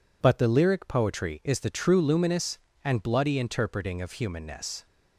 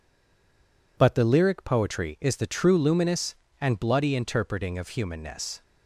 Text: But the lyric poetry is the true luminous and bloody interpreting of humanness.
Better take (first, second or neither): first